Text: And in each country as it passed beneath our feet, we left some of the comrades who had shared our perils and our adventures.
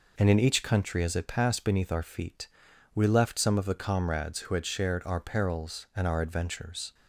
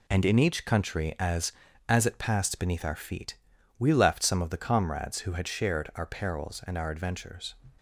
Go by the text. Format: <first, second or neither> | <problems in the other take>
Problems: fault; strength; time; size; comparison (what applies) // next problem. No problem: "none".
first | says "as" twice; at 1.8 s